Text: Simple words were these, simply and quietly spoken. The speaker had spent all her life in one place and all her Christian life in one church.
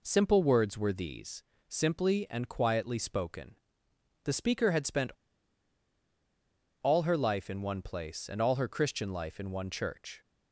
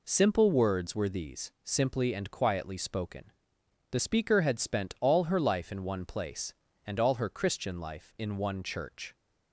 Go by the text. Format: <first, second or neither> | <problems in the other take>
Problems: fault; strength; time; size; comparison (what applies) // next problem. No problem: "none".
second | pauses between "spent" and "all"; strong; at 5.1 s; 1.6 s long